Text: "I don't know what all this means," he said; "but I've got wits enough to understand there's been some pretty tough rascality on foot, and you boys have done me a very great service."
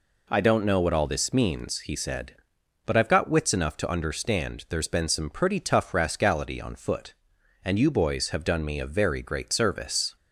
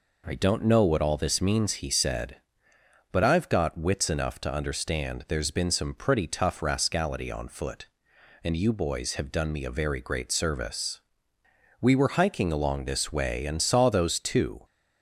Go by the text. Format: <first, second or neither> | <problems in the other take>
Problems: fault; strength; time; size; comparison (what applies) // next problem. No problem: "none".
first | goes on to say "We were hiking along this way and saw those two"; strong; from 11.7 s on; 2.8 s long